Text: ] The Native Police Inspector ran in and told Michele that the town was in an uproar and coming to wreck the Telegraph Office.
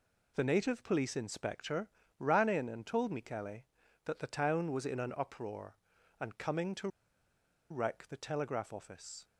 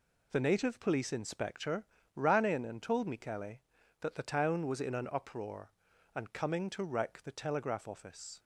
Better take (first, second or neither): second